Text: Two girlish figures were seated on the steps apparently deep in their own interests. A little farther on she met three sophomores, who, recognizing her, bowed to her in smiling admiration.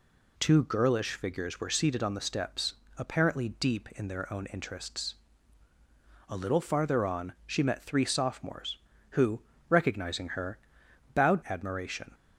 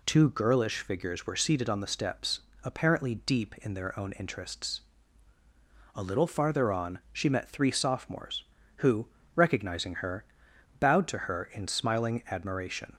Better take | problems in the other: second | pauses between "steps" and "apparently"; slight; at 2.7 s; 0.24 s long; slight in the second // skips "to her in smiling"; at 11.4 s

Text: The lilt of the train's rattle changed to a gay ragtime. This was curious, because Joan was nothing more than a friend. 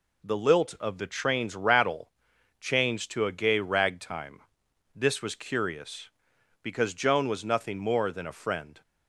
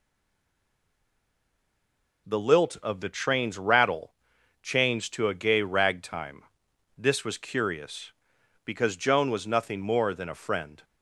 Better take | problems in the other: first | stays silent before the first word; until 2.2 s; 2.2 s long // pauses between "rattle" and "changed"; noticeable; at 4.1 s; 0.48 s long; noticeable in the first

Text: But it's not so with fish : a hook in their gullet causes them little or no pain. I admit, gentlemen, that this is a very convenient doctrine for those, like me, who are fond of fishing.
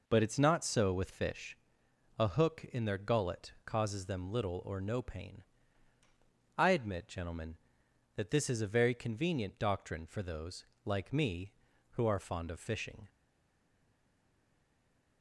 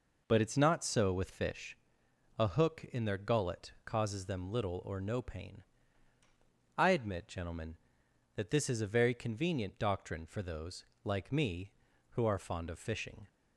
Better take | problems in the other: second | stays silent after the last word; from 13.0 s on; 2.2 s long

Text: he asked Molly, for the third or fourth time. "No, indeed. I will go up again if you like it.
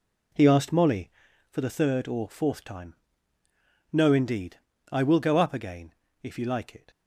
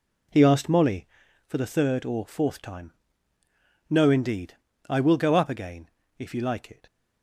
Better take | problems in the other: neither | pauses between "again" and "if"; slight; the same in both

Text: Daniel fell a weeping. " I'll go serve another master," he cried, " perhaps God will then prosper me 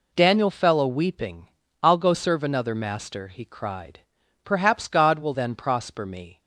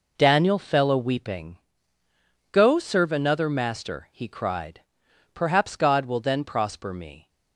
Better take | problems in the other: first | skips "I'll"; at 2.5 s

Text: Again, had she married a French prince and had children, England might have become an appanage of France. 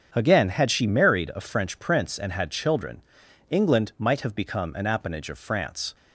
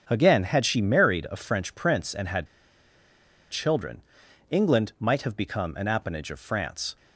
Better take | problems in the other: first | starts louder than the rest; strong; until 1.0 s; 7 dB; strong in the first // pauses between "had" and "children"; at 2.4 s; 1.0 s long

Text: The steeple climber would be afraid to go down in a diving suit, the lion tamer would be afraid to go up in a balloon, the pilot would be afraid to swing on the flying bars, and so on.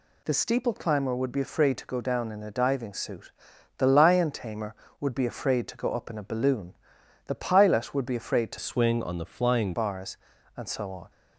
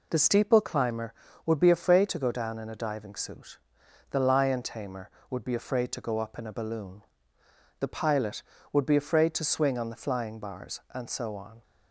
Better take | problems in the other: second | changes voice from "swing" to "flying"; from 8.5 to 9.7 s; 1.2 s long

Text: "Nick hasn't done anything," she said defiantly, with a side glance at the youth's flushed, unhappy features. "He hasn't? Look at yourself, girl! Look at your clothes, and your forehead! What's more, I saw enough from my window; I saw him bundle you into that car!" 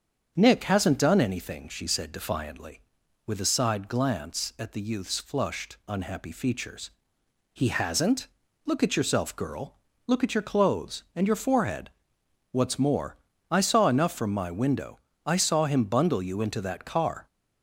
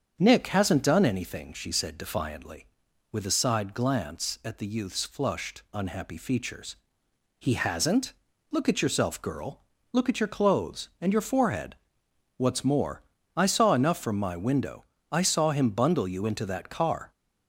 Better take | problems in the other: neither | starts louder than the rest; strong; the same in both

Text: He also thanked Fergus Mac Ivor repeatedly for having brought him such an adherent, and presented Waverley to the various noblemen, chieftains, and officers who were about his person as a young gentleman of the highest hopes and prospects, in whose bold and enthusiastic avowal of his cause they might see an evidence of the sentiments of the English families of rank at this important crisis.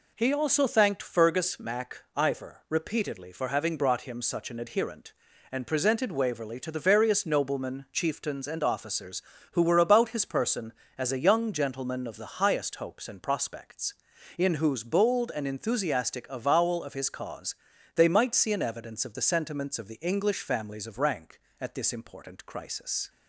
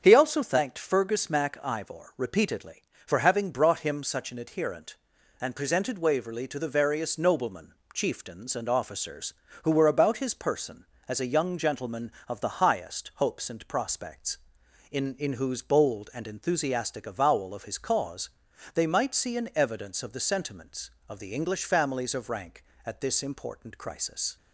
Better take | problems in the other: first | starts louder than the rest; strong; until 1.0 s; 7.5 dB // says "in" twice; at 15.1 s // pauses between "cause" and "they"; noticeable; at 18.2 s; 0.46 s long; also in the first

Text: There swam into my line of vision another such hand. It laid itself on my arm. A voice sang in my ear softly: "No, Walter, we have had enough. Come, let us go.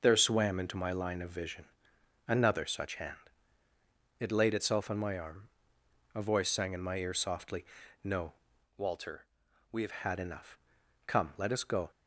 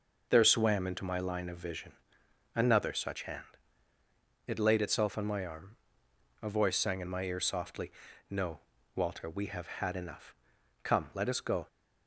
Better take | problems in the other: second | pauses between "vision" and "another"; noticeable; at 1.6 s; 0.64 s long; noticeable in the second // changes voice from "Walter" to "have"; from 8.7 to 9.9 s; 1.2 s long

